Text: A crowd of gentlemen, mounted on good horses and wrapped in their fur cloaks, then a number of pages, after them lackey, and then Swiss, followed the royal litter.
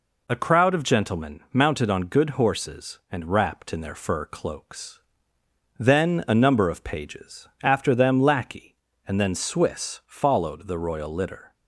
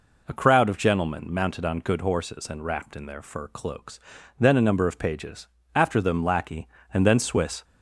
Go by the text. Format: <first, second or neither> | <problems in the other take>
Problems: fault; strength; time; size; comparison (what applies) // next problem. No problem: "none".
first | stops before "followed the royal litter"; at 7.6 s